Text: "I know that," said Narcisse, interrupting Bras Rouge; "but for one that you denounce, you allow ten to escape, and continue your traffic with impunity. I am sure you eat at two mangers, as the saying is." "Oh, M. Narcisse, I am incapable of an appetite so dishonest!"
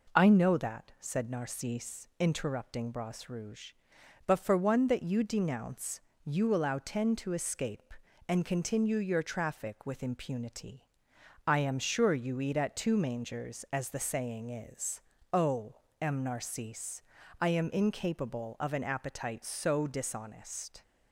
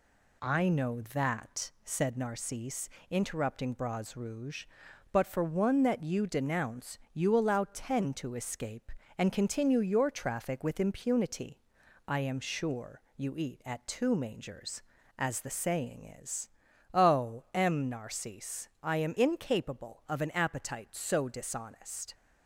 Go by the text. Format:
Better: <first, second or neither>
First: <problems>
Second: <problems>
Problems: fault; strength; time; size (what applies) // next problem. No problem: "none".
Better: neither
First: none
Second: none